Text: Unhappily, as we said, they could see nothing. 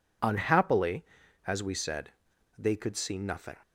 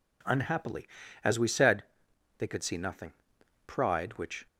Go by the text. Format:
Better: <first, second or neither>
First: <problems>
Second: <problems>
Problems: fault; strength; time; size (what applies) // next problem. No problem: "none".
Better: first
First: none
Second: goes on to say "Pride which"; noticeable; from 3.6 s on; 0.80 s long